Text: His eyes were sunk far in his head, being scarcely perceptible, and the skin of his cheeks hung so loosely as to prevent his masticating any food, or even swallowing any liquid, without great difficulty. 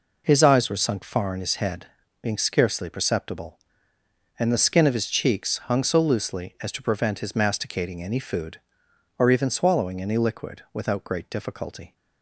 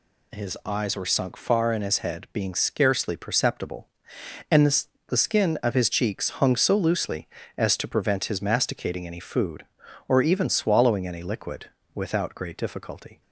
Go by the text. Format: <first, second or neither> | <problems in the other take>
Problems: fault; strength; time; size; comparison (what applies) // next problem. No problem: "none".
first | says "the" twice; at 5.0 s